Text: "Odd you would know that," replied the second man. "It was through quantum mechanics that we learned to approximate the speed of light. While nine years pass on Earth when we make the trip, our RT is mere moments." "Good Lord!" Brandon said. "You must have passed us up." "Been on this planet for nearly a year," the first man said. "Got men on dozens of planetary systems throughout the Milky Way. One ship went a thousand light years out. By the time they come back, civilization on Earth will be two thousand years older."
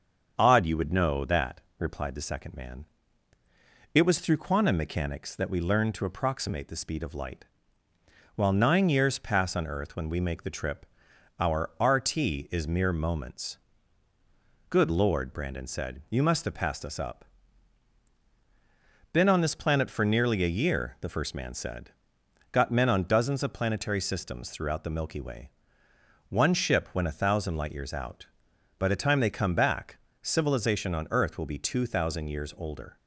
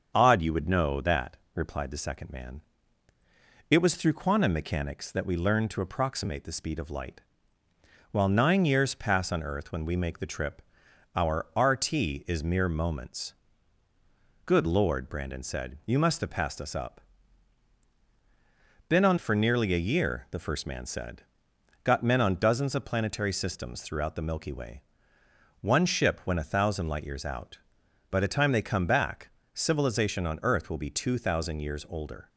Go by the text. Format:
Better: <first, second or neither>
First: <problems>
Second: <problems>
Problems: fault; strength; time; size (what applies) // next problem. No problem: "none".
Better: first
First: starts louder than the rest; until 1.3 s; 7 dB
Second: starts louder than the rest; until 1.1 s; 7 dB // skips "this planet"; at 19.1 s